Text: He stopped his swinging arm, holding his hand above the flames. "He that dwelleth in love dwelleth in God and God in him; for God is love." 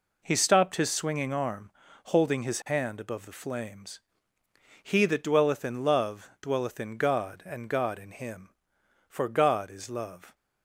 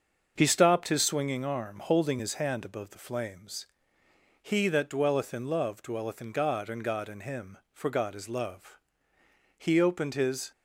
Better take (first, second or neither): first